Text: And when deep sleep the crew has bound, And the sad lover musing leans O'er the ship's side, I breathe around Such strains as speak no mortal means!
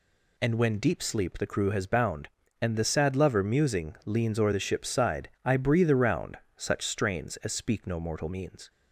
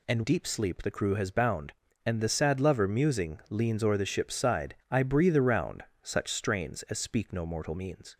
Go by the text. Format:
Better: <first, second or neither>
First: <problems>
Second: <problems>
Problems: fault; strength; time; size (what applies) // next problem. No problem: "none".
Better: first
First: pauses between "around" and "Such"; slight; at 6.3 s; 0.22 s long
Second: skips "when"; at 0.2 s // pauses between "around" and "Such"; slight; at 5.8 s; 0.22 s long